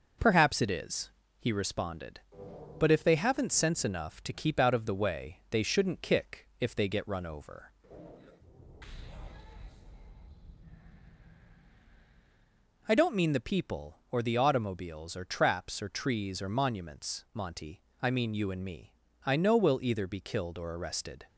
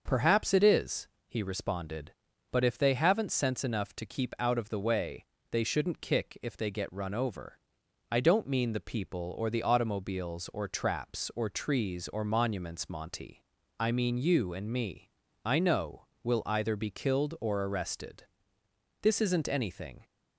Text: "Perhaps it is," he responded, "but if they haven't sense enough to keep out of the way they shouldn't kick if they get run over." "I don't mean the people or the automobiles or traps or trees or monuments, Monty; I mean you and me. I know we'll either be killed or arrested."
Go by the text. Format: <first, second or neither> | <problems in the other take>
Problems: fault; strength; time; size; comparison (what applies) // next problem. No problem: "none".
first | starts louder than the rest; until 1.0 s; 6.5 dB // pauses between "way" and "they"; slight; at 5.2 s; 0.26 s long // pauses between "know" and "we'll"; slight; at 16.0 s; 0.18 s long // goes on to say "This isn't anything"; noticeable; from 19.0 s on; 1.0 s long